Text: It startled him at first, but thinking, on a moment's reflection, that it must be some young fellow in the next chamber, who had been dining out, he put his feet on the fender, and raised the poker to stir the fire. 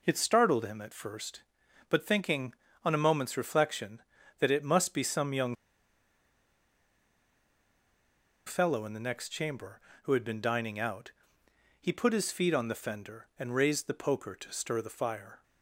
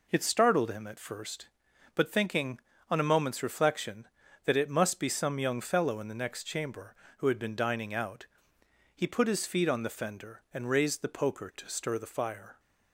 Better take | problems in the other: second | pauses between "young" and "fellow"; strong; at 5.5 s; 2.9 s long

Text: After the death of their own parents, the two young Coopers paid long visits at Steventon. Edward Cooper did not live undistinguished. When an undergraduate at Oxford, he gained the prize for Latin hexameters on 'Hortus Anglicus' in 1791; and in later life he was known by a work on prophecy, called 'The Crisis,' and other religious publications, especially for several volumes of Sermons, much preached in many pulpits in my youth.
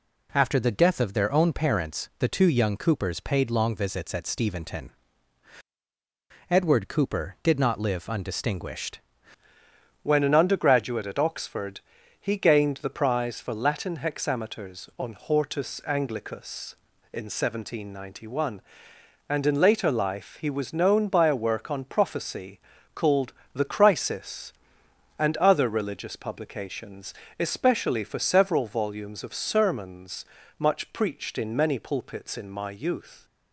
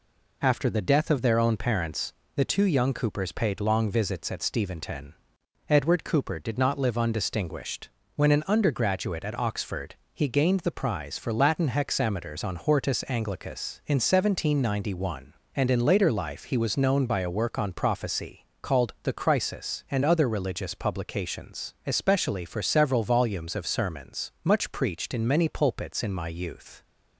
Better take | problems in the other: second | changes voice at "When"; from 10.0 s on; 23.2 s long // pauses between "called" and "The"; slight; at 23.3 s; 0.20 s long

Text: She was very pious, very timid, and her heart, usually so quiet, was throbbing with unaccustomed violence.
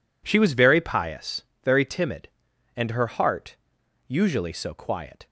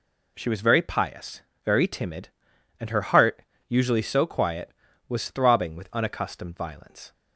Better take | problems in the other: second | stops before "was throbbing with unaccustomed violence"; at 5.2 s

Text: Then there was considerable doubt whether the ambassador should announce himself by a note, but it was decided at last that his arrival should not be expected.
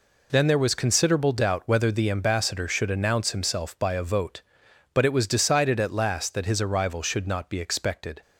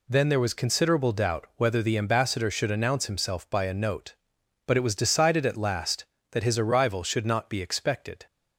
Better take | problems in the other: second | says "vote" for "note"; at 4.0 s

